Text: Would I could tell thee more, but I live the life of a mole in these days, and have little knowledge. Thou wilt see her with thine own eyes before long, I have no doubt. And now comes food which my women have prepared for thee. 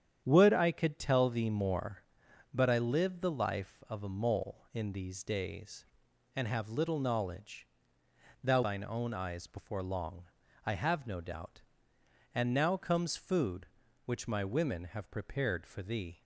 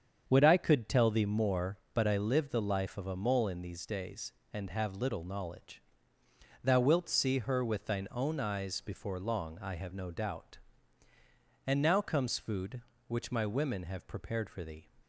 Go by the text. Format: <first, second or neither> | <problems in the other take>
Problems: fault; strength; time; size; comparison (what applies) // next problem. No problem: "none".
second | starts louder than the rest; strong; until 1.2 s; 9 dB; strong in the second // skips "wilt see her with"; at 8.6 s